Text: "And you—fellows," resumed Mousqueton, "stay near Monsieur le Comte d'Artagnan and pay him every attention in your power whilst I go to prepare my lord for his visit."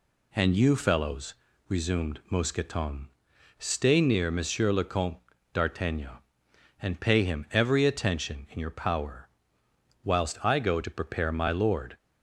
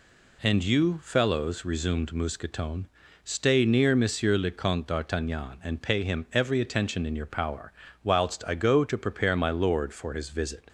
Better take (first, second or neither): second